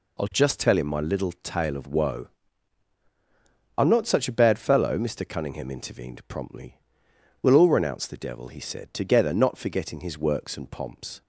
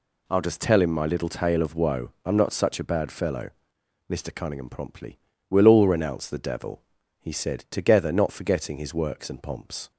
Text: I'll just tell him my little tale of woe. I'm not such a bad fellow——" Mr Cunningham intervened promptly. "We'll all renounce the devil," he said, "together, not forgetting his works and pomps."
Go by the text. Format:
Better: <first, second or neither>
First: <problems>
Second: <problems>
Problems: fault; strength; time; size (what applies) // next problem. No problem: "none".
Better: first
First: none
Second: skips "intervened"; at 4.6 s